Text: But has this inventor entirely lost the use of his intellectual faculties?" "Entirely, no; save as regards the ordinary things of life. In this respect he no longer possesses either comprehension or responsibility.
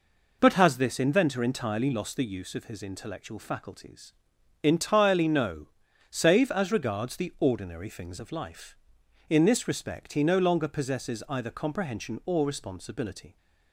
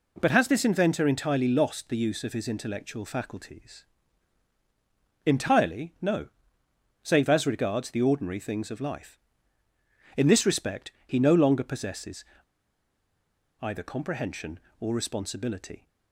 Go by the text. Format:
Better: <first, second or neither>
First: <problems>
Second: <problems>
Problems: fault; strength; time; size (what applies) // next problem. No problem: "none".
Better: first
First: none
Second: pauses between "possesses" and "either"; strong; at 12.2 s; 1.3 s long